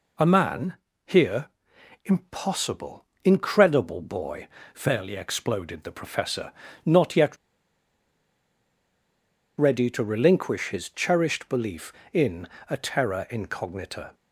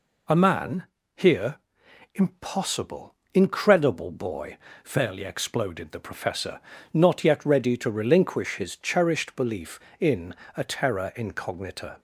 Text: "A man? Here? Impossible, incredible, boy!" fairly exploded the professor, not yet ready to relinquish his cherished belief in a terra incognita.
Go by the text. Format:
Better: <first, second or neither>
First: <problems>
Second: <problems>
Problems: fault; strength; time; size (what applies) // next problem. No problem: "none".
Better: second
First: pauses between "yet" and "ready"; strong; at 7.3 s; 2.2 s long // pauses between "in" and "a"; slight; at 12.4 s; 0.20 s long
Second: pauses between "in" and "a"; slight; at 10.3 s; 0.20 s long